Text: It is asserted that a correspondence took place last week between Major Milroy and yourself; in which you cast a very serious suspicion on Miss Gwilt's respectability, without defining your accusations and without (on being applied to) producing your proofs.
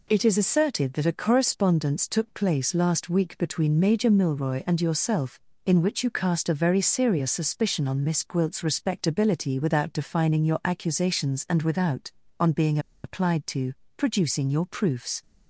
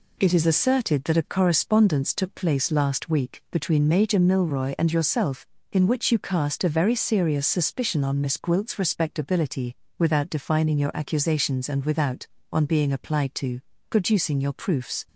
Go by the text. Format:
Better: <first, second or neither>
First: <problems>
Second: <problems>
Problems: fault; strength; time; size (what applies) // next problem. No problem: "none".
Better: second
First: pauses between "being" and "applied"; slight; at 12.7 s; 0.25 s long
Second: none